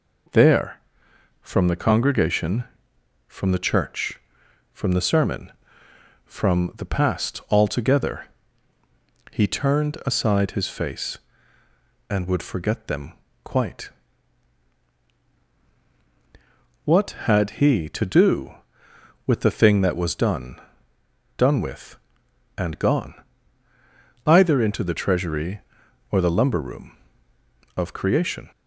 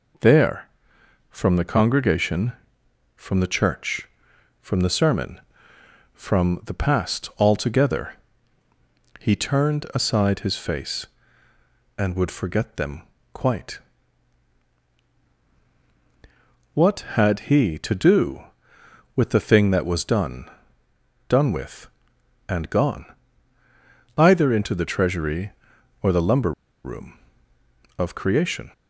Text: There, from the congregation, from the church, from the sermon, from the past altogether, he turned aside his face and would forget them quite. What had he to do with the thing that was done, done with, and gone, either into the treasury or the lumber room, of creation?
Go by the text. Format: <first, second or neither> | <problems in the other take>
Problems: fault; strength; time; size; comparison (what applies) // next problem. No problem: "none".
first | pauses between "them" and "quite"; slight; at 13.0 s; 0.32 s long; slight in the first // pauses between "lumber" and "room"; slight; at 26.5 s; 0.32 s long